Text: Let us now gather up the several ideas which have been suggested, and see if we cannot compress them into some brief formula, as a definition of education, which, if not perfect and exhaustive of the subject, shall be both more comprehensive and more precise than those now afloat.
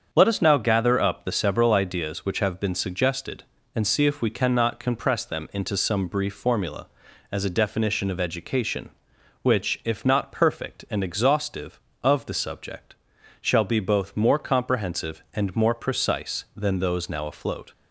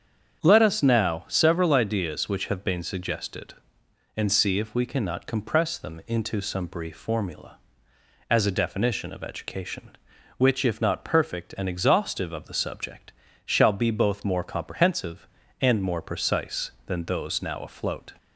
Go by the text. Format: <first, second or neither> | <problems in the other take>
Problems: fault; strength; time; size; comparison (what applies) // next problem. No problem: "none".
first | starts louder than the rest; strong; until 1.4 s; 7.5 dB; strong in the first // skips "gather up the"; at 1.2 s